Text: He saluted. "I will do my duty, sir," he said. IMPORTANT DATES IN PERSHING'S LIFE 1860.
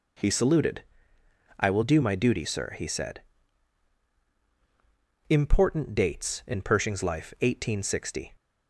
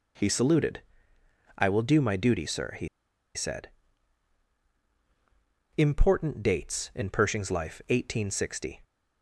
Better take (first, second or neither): first